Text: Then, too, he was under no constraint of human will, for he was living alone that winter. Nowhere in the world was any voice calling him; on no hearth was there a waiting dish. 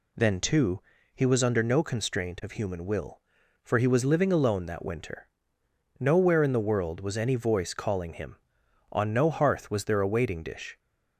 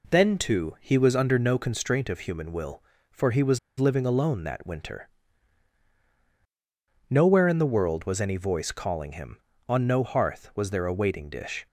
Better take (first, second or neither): first